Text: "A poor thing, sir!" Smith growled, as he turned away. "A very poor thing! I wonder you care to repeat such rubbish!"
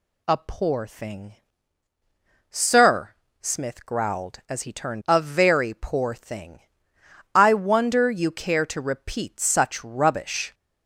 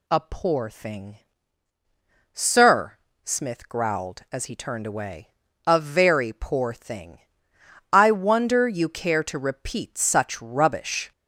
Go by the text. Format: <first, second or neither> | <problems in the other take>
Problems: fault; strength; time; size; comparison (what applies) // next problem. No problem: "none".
second | skips "away"; at 5.0 s